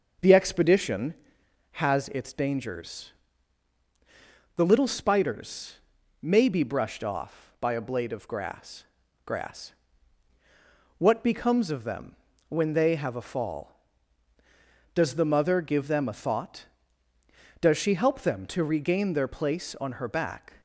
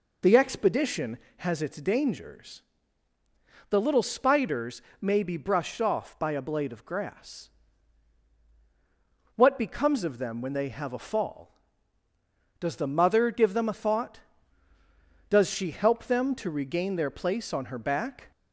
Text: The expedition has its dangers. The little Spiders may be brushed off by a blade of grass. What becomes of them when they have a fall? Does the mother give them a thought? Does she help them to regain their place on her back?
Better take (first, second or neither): second